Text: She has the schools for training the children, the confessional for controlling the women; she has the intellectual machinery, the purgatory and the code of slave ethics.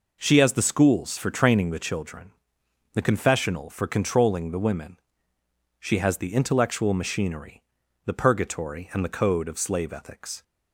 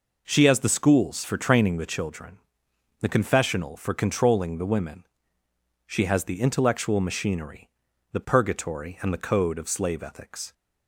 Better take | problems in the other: neither | none

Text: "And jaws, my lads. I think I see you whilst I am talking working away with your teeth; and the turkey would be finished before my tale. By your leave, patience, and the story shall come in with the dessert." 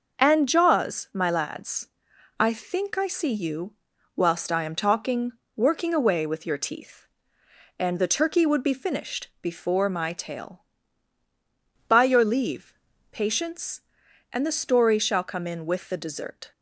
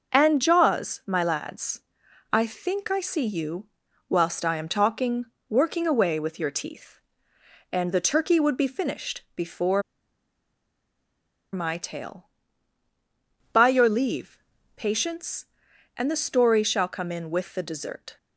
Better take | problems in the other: first | pauses between "you" and "whilst"; at 3.6 s; 0.42 s long; also in the first // pauses between "talking" and "working"; slight; at 5.2 s; 0.24 s long; slight in the first // pauses between "before" and "my"; strong; at 9.8 s; 1.7 s long

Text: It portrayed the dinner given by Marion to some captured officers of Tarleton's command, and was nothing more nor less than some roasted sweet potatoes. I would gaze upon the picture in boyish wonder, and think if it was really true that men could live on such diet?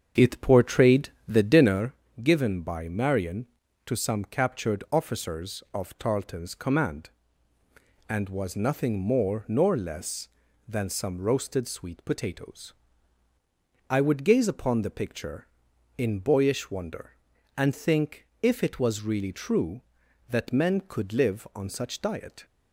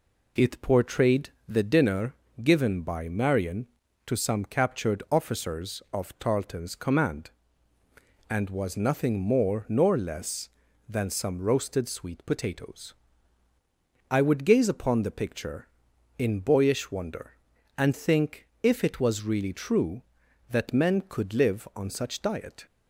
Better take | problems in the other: second | starts louder than the rest; strong; until 1.9 s; 7 dB // pauses between "portrayed" and "the"; slight; at 1.1 s; 0.18 s long; slight in the second // pauses between "dinner" and "given"; slight; at 1.9 s; 0.30 s long; slight in the second // pauses between "think" and "if"; slight; at 18.2 s; 0.16 s long; slight in the second

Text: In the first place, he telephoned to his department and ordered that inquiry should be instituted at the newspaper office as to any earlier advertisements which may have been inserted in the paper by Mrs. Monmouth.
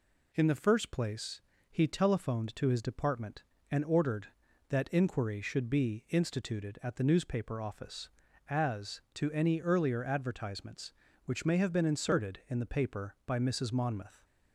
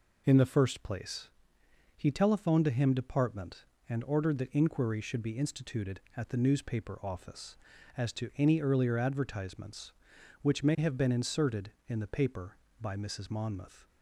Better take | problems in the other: first | says "him" for "his"; at 2.6 s

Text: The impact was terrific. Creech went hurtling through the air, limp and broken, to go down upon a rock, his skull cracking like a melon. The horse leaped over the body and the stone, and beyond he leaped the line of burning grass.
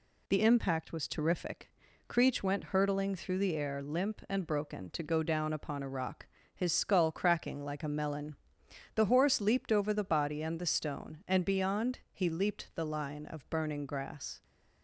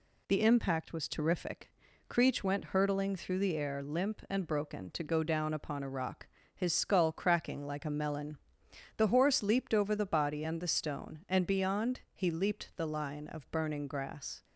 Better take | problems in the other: neither | none

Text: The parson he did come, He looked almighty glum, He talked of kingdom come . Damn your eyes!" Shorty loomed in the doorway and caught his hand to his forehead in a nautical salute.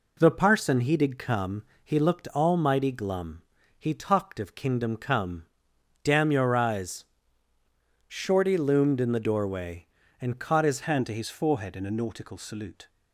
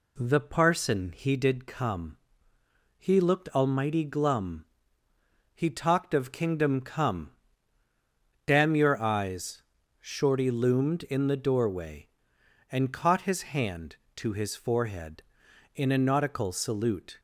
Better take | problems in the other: second | changes voice at "hand"; from 10.8 s on; 2.0 s long

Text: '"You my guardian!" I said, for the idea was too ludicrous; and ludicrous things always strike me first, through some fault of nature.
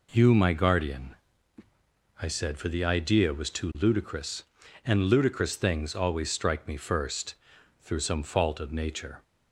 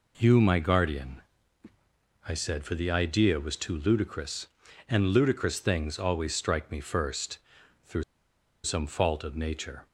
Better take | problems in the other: first | pauses between "through" and "some"; noticeable; at 8.0 s; 0.60 s long

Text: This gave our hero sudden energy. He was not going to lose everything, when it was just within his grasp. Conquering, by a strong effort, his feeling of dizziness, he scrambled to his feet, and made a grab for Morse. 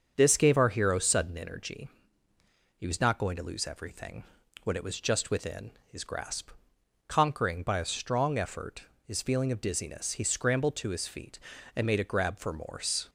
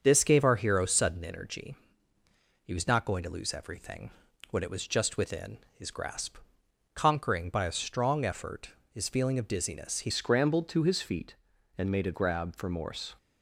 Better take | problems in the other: first | starts louder than the rest; until 1.0 s; 7 dB; also in the first // pauses between "within" and "his"; slight; at 5.5 s; 0.18 s long; slight in the first // changes voice at "scrambled"; from 10.0 s on; 3.1 s long

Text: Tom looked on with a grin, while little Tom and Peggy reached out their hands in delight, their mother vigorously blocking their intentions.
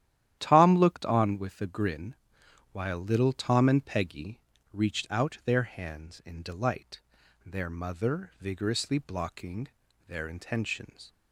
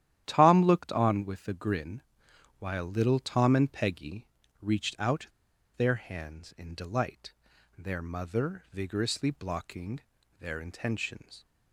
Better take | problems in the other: first | starts louder than the rest; strong; until 1.2 s; 11.5 dB; strong in the first // pauses between "Peggy" and "reached"; slight; at 4.2 s; 0.36 s long; slight in the first // pauses between "out" and "their"; noticeable; at 5.2 s; 0.51 s long // pauses between "blocking" and "their"; at 10.0 s; 0.40 s long; also in the first

